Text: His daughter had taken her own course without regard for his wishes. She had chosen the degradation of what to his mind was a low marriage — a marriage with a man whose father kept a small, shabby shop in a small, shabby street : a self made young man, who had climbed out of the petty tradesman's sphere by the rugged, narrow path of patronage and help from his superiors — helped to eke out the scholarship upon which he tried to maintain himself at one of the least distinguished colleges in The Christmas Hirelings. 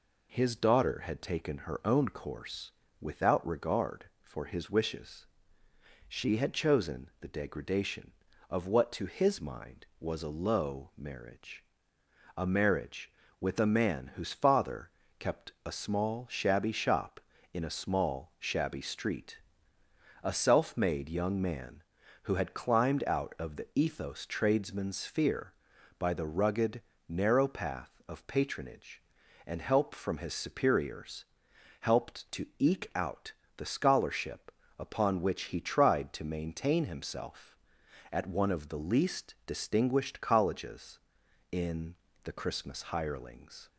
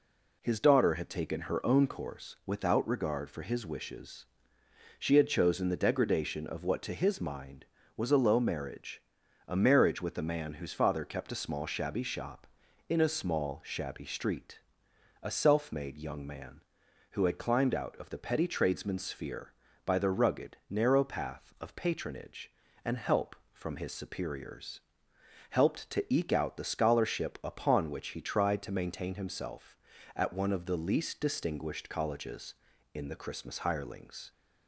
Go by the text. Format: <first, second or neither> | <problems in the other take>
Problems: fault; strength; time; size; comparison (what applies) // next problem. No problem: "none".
second | pauses between "course" and "without"; slight; at 2.6 s; 0.30 s long // pauses between "father" and "kept"; slight; at 14.9 s; 0.26 s long // says "ethos" for "petty"; at 23.7 s // pauses between "out" and "the"; slight; at 33.3 s; 0.24 s long // pauses between "scholarship" and "upon"; slight; at 34.5 s; 0.26 s long // pauses between "in" and "The"; slight; at 41.9 s; 0.30 s long